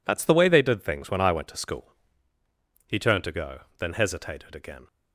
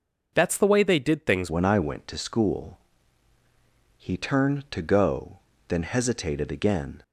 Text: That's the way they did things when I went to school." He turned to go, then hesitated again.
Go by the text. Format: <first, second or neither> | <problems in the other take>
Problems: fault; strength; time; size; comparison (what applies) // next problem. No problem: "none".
first | changes voice at "when"; from 1.4 s on; 5.6 s long